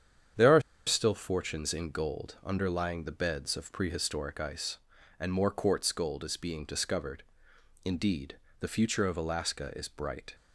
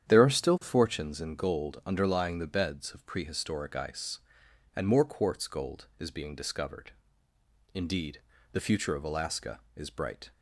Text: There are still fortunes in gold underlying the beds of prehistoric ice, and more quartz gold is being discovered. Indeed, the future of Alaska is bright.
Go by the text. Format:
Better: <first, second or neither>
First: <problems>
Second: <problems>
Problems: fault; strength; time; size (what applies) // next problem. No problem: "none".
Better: second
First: starts louder than the rest; strong; until 1.6 s; 8.5 dB // pauses between "are" and "still"; slight; at 0.6 s; 0.26 s long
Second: starts louder than the rest; strong; until 1.1 s; 9 dB